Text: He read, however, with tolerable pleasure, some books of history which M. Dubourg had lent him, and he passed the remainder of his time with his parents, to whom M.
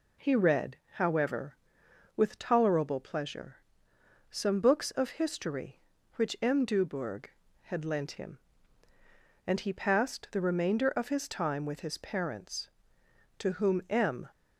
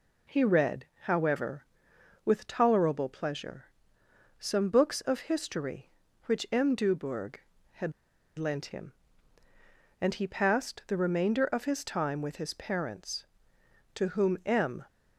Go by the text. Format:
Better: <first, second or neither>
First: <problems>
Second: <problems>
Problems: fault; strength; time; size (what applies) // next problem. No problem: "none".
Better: first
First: none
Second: pauses between "had" and "lent"; noticeable; at 7.9 s; 0.46 s long